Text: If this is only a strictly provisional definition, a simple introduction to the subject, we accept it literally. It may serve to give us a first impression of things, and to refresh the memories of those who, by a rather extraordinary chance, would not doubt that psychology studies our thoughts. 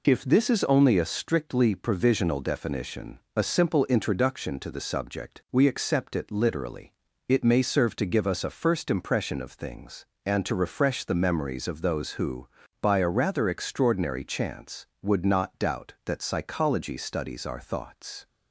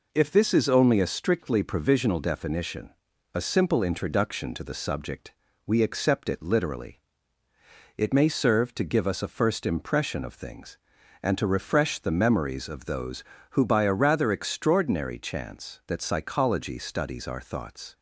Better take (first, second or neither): first